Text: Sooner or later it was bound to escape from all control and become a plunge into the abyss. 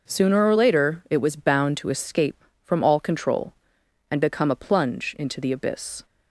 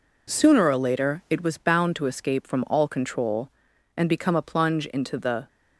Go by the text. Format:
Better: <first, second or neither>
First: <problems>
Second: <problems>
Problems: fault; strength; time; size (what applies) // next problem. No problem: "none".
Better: first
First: none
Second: stops before "abyss"; at 5.4 s